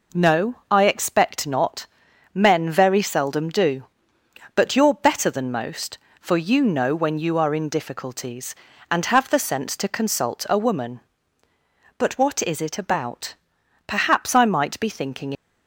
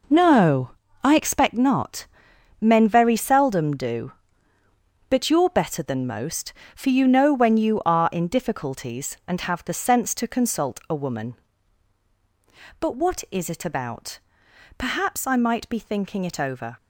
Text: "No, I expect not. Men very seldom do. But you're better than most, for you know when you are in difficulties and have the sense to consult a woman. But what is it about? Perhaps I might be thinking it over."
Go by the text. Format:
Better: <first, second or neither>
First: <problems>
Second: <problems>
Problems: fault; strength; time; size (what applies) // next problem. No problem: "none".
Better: second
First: stops before "it over"; at 15.3 s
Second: none